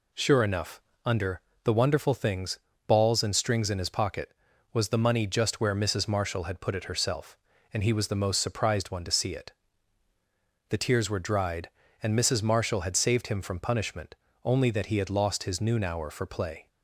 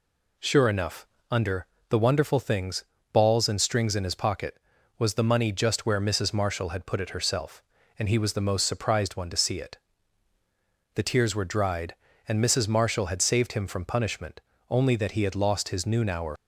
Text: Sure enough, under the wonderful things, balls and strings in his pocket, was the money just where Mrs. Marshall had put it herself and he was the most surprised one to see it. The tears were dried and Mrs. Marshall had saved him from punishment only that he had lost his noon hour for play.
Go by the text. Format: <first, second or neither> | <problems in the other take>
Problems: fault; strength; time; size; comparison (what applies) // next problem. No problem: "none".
first | pauses between "under" and "the"; slight; at 1.6 s; 0.24 s long; slight in the first // pauses between "punishment" and "only"; slight; at 14.3 s; 0.30 s long; slight in the first // stops before "for play"; at 16.3 s